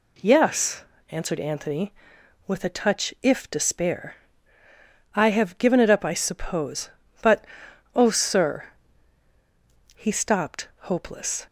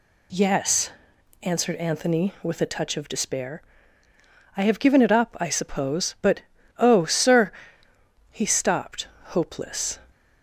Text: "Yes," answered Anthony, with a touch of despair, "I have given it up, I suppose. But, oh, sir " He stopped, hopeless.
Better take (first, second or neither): second